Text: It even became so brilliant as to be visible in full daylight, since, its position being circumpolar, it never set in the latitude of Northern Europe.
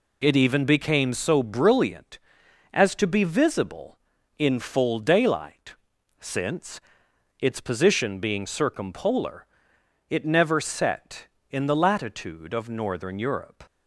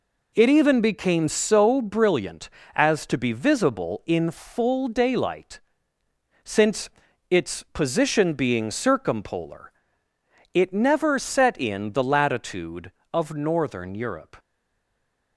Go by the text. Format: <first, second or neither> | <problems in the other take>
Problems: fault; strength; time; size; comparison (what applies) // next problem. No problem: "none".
first | stays silent after the last word; slight; from 14.3 s on; 1.0 s long